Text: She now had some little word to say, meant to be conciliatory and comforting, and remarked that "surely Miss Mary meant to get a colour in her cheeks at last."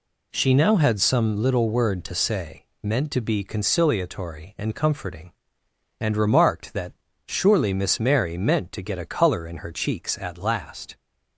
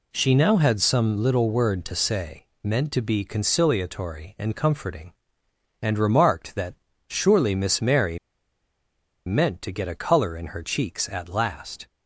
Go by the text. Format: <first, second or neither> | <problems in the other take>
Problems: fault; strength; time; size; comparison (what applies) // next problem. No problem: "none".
first | pauses between "that" and "surely"; slight; at 6.7 s; 0.32 s long; slight in the first // pauses between "Mary" and "meant"; at 8.1 s; 1.0 s long